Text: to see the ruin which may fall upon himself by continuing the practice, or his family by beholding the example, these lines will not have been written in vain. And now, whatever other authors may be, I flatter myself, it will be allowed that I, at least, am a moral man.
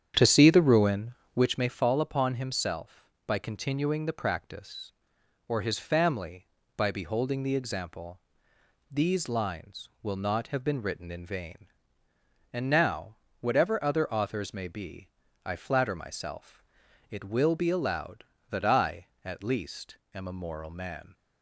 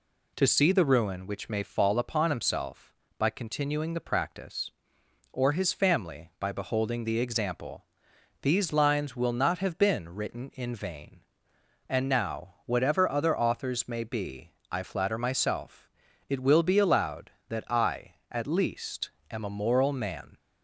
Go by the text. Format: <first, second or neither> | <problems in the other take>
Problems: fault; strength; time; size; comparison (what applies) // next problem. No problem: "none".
second | starts louder than the rest; strong; until 1.5 s; 9 dB